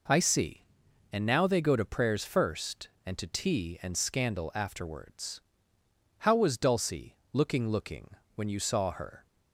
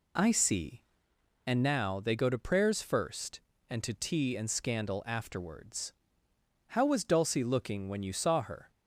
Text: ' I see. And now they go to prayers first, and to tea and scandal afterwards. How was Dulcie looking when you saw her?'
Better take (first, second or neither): second